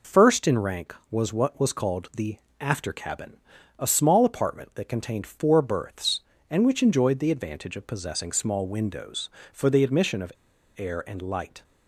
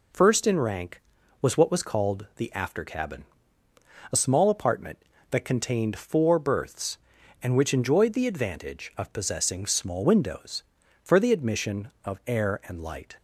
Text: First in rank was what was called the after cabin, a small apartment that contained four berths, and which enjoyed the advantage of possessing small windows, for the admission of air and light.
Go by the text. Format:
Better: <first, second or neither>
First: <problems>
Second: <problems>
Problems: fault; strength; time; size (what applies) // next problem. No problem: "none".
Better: second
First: pauses between "the" and "after"; slight; at 2.3 s; 0.22 s long // pauses between "of" and "air"; at 10.3 s; 0.45 s long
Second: none